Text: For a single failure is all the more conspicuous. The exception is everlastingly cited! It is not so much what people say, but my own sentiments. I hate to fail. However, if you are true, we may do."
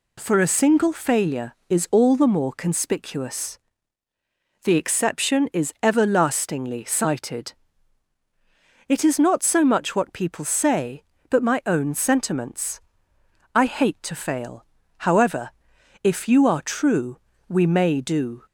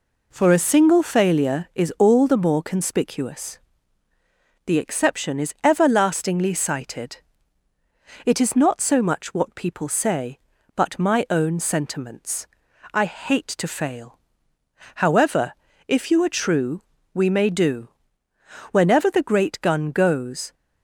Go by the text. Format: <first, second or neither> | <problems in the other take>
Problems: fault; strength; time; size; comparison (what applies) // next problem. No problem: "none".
first | goes on to say "Whenever the great gun goes"; strong; from 18.7 s on; 1.8 s long